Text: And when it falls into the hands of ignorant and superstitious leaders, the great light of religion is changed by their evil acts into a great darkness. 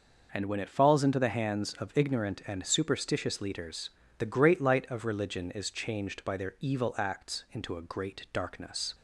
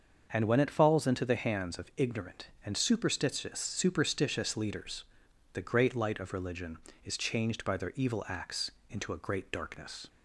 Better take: first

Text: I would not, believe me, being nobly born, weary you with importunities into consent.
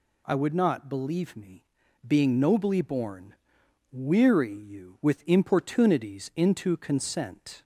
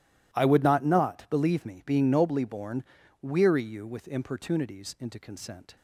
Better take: first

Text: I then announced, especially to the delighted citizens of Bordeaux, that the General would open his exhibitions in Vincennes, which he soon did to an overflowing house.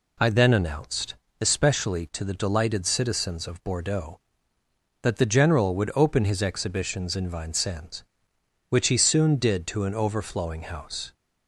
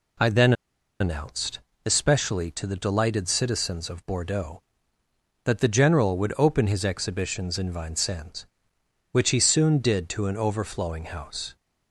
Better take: first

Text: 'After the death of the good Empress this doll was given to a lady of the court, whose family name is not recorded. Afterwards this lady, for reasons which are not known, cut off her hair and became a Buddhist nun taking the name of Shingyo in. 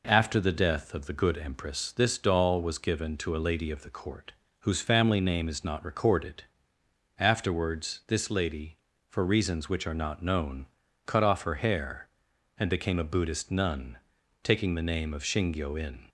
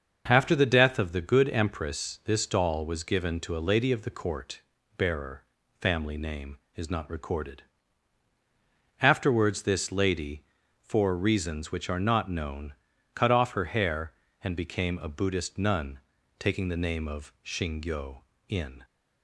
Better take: first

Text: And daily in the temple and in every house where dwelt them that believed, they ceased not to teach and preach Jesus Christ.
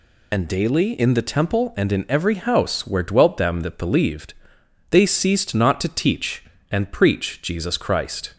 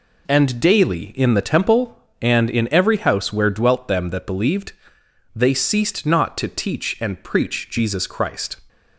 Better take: second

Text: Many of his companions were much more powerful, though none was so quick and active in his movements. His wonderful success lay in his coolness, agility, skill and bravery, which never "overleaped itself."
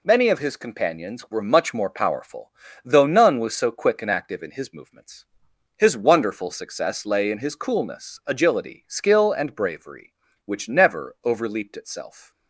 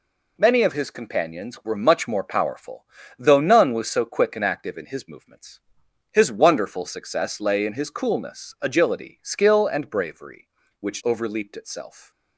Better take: first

